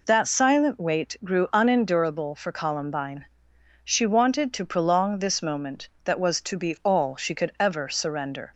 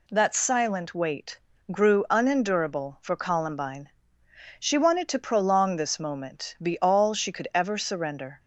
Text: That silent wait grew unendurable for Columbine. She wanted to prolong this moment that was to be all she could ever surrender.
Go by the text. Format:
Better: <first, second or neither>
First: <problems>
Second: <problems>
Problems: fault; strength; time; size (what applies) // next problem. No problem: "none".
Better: first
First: none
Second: pauses between "wait" and "grew"; slight; at 1.4 s; 0.32 s long // skips "that was to"; at 6.5 s